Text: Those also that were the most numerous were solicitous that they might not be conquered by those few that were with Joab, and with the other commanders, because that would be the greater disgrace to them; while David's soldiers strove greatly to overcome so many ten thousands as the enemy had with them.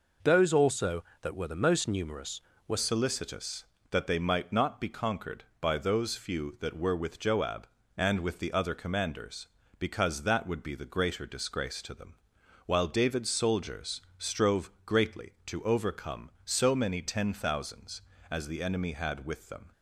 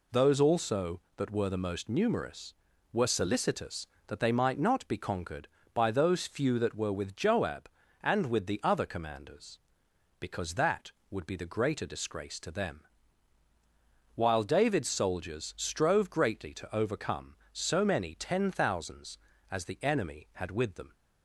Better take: second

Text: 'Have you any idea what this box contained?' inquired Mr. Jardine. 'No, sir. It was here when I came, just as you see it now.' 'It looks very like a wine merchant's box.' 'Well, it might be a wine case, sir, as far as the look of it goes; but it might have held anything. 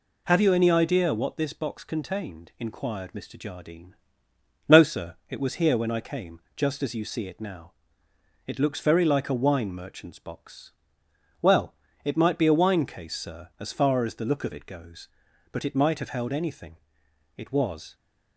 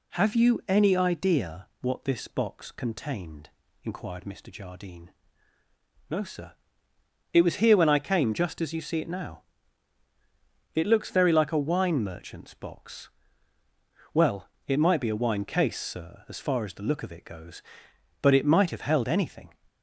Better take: second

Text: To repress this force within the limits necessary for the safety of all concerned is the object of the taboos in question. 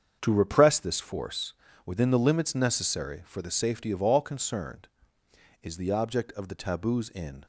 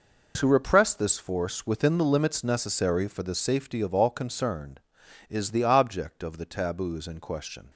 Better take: second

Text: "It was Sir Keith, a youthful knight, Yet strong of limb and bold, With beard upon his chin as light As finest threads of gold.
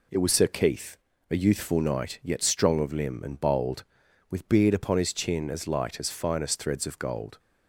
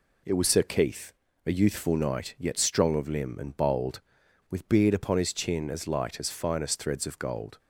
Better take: neither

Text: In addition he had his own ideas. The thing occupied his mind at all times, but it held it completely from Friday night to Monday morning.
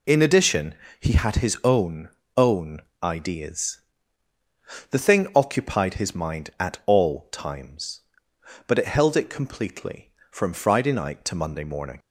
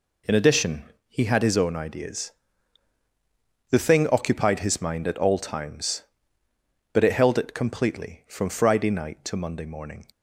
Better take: second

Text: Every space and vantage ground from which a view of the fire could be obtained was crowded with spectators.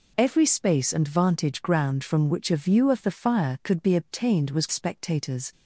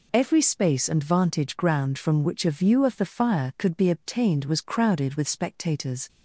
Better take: second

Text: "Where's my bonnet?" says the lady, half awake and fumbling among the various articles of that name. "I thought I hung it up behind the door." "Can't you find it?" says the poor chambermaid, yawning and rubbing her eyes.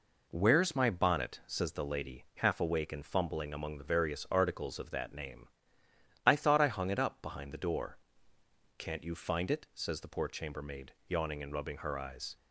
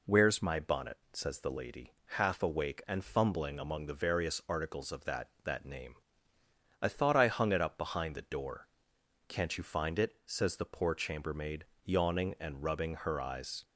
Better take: first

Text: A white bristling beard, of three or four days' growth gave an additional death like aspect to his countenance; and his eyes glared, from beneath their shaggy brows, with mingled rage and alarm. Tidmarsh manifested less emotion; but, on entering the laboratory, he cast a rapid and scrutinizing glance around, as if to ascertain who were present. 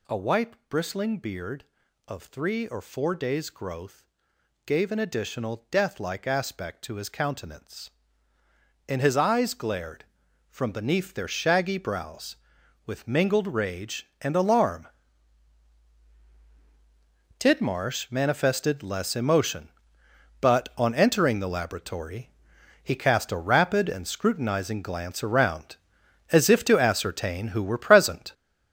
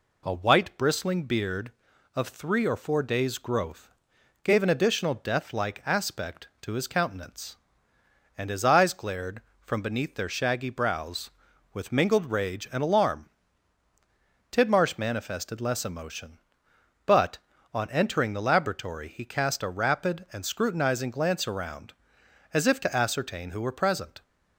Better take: second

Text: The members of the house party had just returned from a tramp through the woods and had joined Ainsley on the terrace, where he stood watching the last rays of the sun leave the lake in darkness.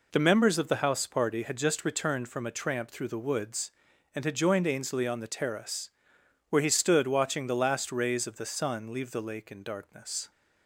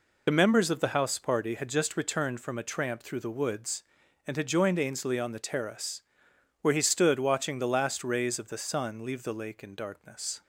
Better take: first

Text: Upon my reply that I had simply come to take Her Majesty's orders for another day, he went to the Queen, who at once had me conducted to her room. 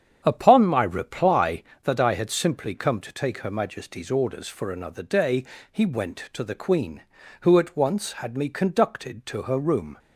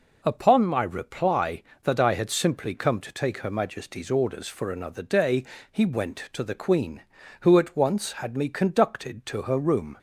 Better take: second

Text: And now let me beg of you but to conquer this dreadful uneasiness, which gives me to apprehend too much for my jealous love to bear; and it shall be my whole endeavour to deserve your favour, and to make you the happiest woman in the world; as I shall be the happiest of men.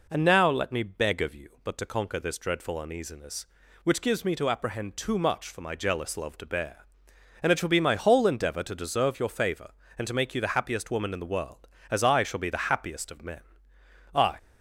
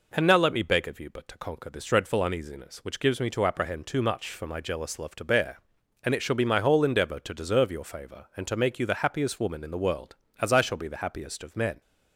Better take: second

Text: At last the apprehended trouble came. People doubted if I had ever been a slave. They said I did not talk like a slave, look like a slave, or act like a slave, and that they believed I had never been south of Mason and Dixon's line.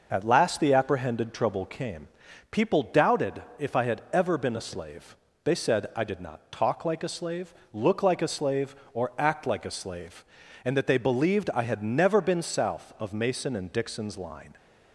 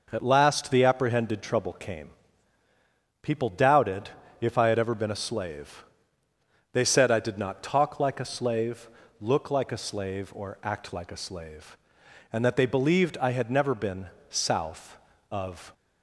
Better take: first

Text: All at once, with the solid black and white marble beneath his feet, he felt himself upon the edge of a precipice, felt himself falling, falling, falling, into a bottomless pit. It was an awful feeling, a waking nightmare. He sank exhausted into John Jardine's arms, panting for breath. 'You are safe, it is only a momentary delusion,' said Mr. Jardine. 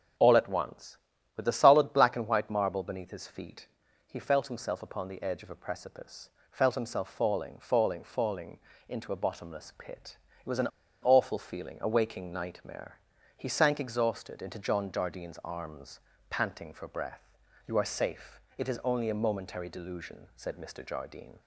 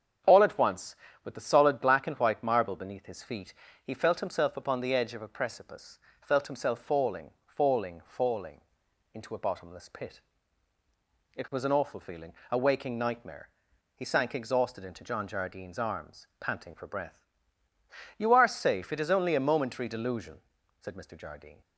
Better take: second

